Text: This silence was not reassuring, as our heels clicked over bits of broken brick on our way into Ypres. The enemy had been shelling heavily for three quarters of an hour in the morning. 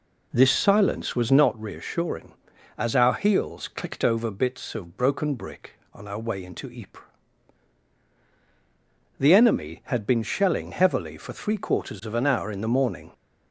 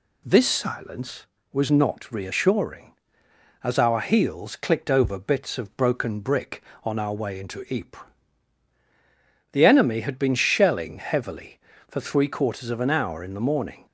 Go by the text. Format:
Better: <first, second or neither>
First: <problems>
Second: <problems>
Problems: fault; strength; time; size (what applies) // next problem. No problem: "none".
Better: second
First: starts louder than the rest; until 1.5 s; 3.5 dB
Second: none